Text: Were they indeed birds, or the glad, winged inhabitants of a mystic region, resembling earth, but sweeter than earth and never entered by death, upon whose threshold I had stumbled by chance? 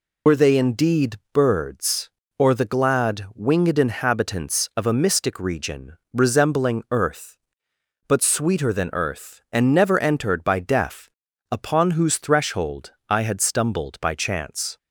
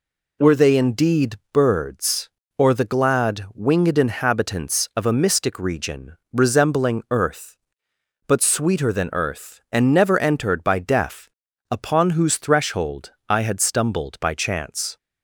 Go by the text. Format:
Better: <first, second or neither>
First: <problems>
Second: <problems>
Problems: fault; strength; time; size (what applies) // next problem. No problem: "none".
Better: second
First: loses the start of "Were"; at 0.2 s; 55 ms // pauses between "indeed" and "birds"; slight; at 1.1 s; 0.16 s long // pauses between "threshold" and "I"; slight; at 12.9 s; 0.16 s long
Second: pauses between "indeed" and "birds"; slight; at 1.3 s; 0.16 s long // pauses between "threshold" and "I"; slight; at 13.1 s; 0.16 s long